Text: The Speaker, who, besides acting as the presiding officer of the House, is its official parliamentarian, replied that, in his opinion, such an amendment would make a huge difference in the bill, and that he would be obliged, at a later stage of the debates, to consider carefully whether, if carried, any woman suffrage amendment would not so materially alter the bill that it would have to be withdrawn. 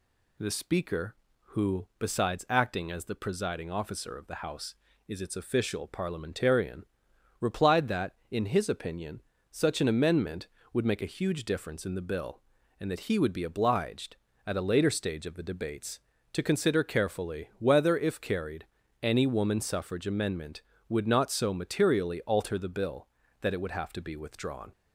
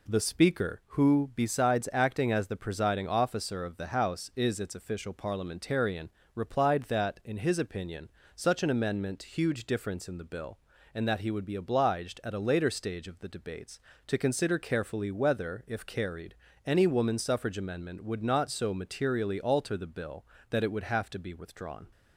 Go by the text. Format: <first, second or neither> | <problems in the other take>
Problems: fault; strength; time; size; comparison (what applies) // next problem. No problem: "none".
first | skips "would make a"; at 9.2 s